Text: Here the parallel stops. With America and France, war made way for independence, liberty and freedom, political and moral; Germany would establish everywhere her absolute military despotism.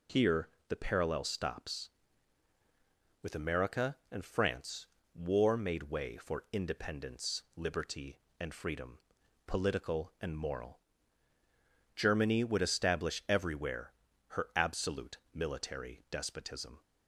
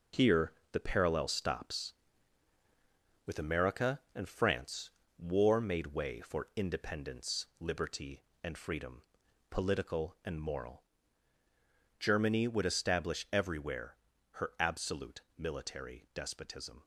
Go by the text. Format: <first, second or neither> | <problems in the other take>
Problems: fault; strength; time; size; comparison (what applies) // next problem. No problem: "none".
first | gets quieter; strong; throughout; 7 dB // pauses between "Here" and "the"; slight; at 0.5 s; 0.18 s long; slight in the first // pauses between "everywhere" and "her"; at 13.9 s; 0.38 s long; also in the first